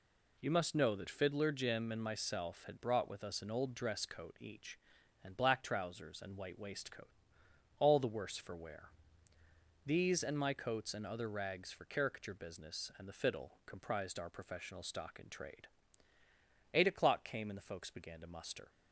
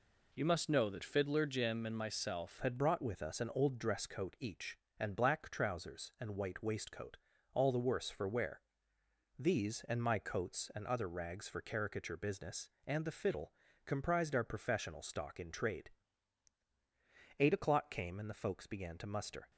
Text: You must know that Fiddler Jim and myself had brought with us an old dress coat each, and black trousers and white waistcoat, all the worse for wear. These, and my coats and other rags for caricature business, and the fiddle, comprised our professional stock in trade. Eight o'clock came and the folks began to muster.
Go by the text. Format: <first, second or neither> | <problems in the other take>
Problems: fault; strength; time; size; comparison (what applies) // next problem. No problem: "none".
first | changes voice at "had"; from 2.6 s on; 16.9 s long